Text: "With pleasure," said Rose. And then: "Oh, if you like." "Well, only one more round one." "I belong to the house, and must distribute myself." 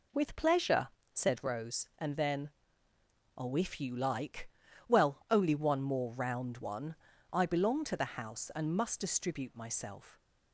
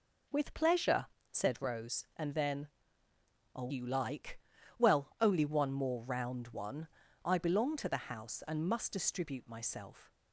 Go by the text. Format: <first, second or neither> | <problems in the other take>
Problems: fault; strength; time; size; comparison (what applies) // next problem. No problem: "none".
first | skips "if"; at 3.7 s